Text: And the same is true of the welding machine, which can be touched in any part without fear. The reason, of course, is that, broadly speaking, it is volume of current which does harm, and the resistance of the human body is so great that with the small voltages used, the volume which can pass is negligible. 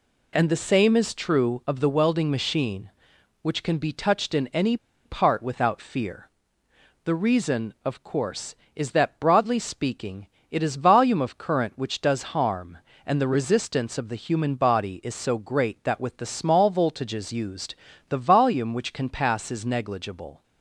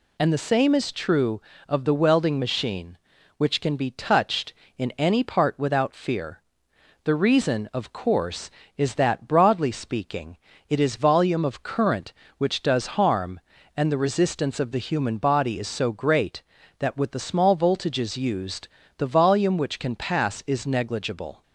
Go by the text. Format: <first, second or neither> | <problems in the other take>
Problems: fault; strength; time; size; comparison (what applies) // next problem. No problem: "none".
second | pauses between "any" and "part"; slight; at 4.7 s; 0.29 s long